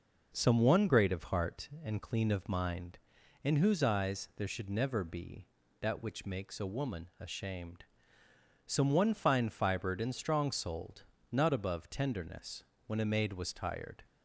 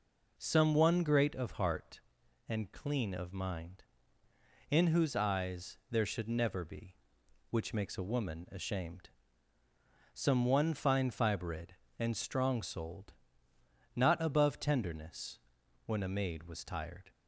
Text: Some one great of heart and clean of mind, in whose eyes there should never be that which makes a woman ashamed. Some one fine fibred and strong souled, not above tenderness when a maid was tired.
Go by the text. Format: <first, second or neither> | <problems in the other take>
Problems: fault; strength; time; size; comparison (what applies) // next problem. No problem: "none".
first | skips "that"; at 7.2 s // pauses between "tenderness" and "when"; noticeable; at 15.3 s; 0.48 s long; slight in the first